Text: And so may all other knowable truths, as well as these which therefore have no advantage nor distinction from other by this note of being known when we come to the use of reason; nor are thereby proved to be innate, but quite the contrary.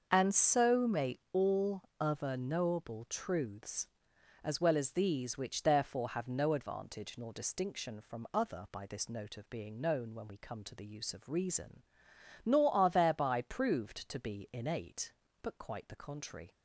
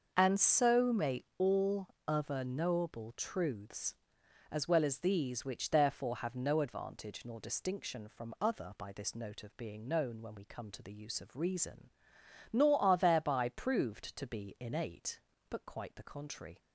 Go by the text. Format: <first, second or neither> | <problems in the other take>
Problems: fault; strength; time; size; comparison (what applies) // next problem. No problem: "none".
neither | starts louder than the rest; the same in both // pauses between "all" and "other"; slight; the same in both